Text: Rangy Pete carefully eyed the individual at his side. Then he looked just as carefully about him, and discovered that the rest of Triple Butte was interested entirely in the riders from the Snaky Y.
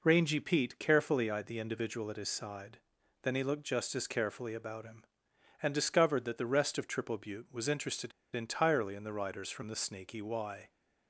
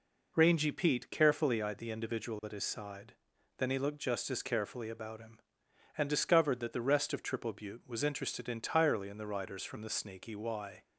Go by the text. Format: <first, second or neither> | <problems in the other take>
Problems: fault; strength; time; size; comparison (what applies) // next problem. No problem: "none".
second | pauses between "interested" and "entirely"; slight; at 8.1 s; 0.23 s long